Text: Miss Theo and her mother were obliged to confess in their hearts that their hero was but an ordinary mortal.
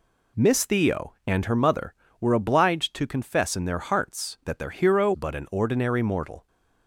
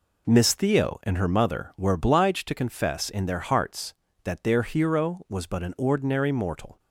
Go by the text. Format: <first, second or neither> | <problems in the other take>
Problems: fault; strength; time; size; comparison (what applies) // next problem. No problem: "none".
second | skips "was"; at 5.1 s